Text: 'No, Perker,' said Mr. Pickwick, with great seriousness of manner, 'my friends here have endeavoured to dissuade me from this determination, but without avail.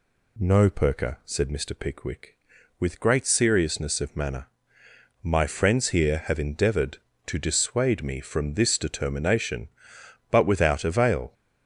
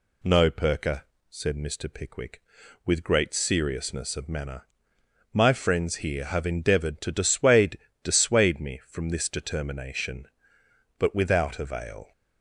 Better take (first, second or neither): first